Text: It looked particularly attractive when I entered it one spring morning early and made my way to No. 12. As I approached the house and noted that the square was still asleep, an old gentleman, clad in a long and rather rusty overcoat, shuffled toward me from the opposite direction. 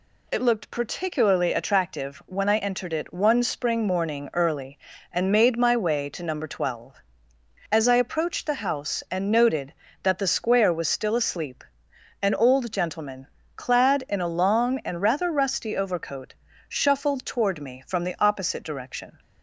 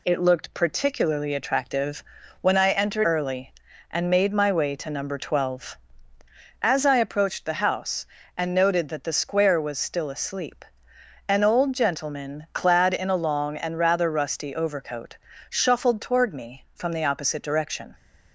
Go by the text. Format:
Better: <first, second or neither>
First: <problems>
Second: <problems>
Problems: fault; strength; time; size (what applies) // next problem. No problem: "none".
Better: first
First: none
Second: pauses between "attractive" and "when"; at 2.0 s; 0.38 s long // skips "it one spring morning"; at 3.0 s